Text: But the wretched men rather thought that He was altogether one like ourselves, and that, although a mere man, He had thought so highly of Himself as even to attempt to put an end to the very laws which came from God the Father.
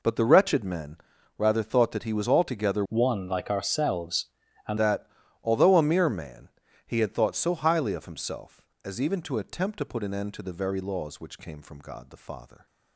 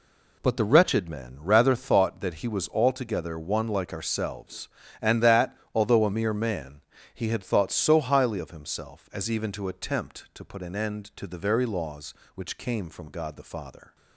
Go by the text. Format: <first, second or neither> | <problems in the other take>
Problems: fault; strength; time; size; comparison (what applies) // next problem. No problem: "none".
second | pauses between "men" and "rather"; at 0.9 s; 0.40 s long // changes voice from "one" to "and"; from 2.8 to 4.7 s; 1.9 s long